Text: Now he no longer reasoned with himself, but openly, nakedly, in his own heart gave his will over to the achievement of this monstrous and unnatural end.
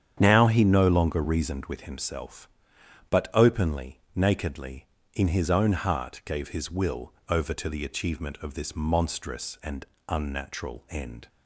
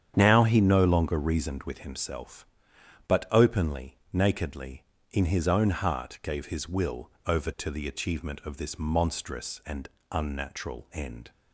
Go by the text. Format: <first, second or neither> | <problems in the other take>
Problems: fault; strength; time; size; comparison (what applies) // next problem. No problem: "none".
neither | starts louder than the rest; strong; the same in both // pauses between "will" and "over"; slight; the same in both // pauses between "and" and "unnatural"; slight; the same in both